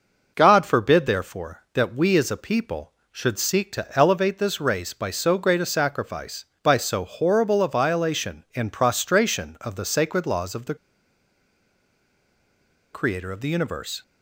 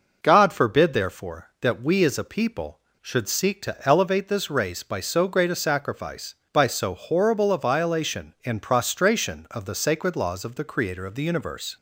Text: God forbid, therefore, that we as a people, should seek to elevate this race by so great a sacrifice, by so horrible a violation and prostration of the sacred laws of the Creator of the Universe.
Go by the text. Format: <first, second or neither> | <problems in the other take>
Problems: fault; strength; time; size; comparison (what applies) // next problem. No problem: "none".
second | pauses between "the" and "Creator"; strong; at 10.7 s; 2.1 s long